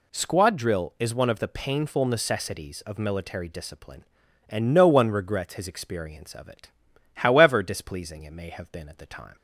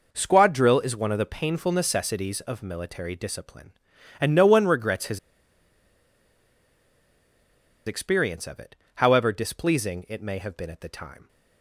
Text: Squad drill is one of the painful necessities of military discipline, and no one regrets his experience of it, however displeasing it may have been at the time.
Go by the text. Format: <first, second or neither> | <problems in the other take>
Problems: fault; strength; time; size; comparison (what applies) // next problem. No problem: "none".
first | pauses between "his" and "experience"; strong; at 5.1 s; 2.6 s long